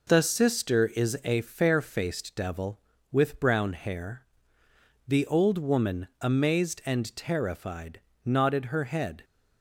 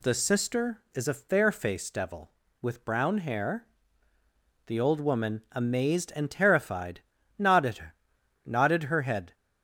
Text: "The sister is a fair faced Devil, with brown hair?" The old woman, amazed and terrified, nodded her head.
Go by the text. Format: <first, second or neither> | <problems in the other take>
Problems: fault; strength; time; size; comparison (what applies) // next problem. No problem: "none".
first | says "nodded" twice; at 8.4 s